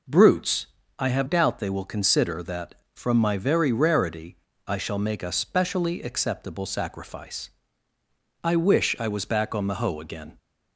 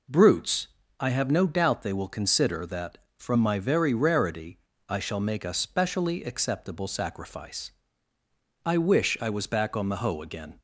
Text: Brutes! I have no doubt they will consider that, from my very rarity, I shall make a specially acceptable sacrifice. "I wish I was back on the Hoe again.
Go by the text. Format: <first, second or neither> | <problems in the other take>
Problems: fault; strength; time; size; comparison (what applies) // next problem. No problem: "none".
second | skips "no"; at 1.2 s